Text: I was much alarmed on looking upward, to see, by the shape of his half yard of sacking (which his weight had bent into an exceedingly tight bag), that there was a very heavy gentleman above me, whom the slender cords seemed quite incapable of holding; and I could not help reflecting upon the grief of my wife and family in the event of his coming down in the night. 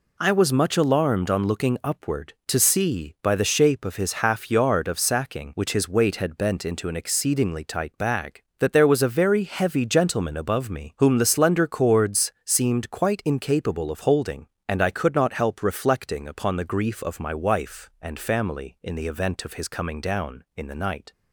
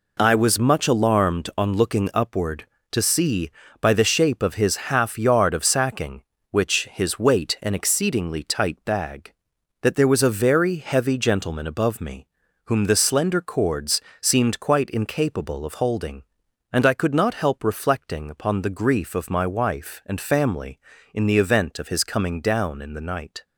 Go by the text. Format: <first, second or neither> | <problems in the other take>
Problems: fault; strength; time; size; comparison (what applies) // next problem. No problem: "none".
first | skips "had bent into"; at 7.5 s // pauses between "cords" and "seemed"; slight; at 14.0 s; 0.20 s long